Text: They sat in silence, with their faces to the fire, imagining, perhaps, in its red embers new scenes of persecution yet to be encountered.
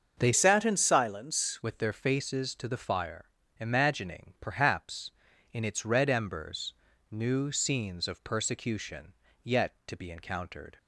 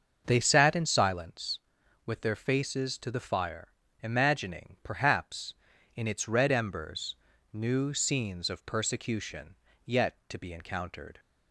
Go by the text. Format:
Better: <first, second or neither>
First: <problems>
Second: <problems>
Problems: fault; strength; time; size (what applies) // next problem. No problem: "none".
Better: second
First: starts louder than the rest; until 1.1 s; 6.5 dB // changes voice from "sat" to "silence"; from 0.3 to 1.6 s; 1.3 s long // pauses between "embers" and "new"; slight; at 6.7 s; 0.36 s long // pauses between "persecution" and "yet"; slight; at 9.1 s; 0.30 s long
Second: starts louder than the rest; until 1.2 s; 6.5 dB // pauses between "embers" and "new"; slight; at 7.1 s; 0.36 s long // pauses between "persecution" and "yet"; slight; at 9.5 s; 0.30 s long